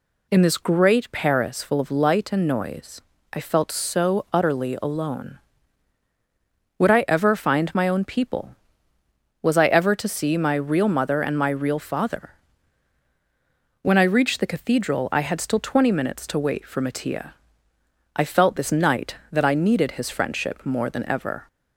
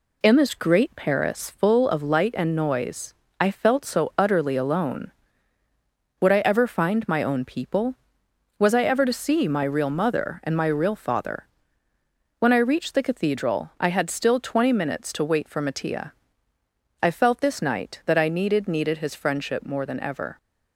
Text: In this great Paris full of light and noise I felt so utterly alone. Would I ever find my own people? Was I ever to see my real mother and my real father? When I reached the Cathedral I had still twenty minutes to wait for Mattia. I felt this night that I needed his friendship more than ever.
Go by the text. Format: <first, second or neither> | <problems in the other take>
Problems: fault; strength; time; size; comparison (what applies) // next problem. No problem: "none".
first | pauses between "noise" and "I"; slight; at 3.1 s; 0.26 s long; slight in the first // says "needed" twice; at 18.6 s